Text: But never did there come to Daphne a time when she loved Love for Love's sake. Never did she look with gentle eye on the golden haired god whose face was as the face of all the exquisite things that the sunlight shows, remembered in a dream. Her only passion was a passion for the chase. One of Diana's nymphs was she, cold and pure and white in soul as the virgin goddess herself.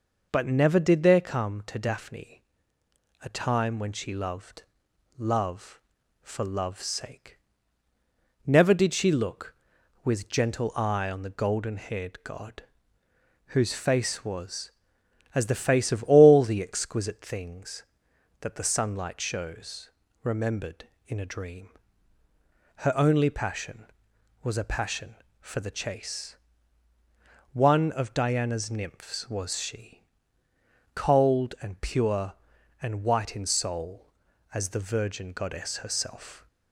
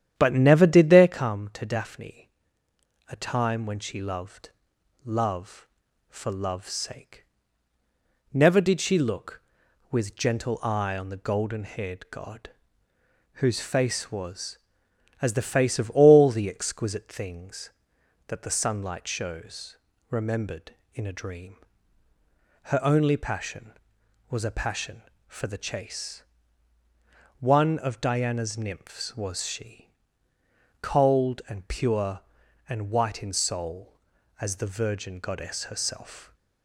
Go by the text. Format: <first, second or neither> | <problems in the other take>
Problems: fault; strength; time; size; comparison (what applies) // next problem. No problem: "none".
first | starts louder than the rest; strong; until 1.3 s; 10 dB // pauses between "Daphne" and "a"; noticeable; at 2.2 s; 0.78 s long; noticeable in the first // pauses between "loved" and "Love"; noticeable; at 4.4 s; 0.54 s long; noticeable in the first // pauses between "god" and "whose"; noticeable; at 12.4 s; 0.84 s long; noticeable in the first